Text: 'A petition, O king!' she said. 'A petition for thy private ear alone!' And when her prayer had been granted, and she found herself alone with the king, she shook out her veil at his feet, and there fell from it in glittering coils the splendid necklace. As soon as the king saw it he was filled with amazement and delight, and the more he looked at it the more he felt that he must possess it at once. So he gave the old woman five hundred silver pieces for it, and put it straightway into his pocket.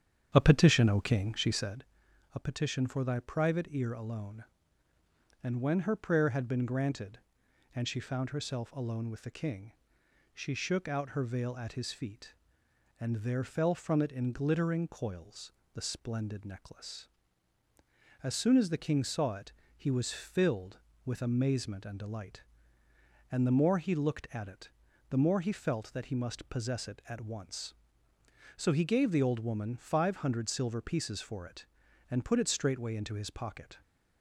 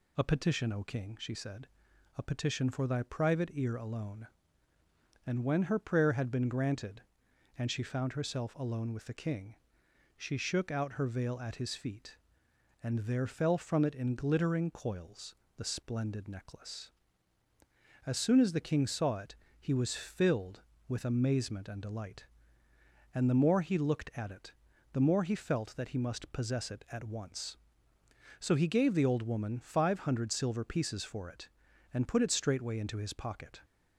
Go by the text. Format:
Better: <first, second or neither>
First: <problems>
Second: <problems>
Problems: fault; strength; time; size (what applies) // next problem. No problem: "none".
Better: second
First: starts louder than the rest; strong; until 1.8 s; 8.5 dB // pauses between "coils" and "the"; slight; at 15.5 s; 0.22 s long // pauses between "it" and "he"; slight; at 19.5 s; 0.24 s long // pauses between "it" and "the"; at 24.6 s; 0.40 s long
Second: pauses between "coils" and "the"; slight; at 15.3 s; 0.22 s long // pauses between "it" and "he"; slight; at 19.3 s; 0.24 s long // pauses between "it" and "the"; at 24.5 s; 0.40 s long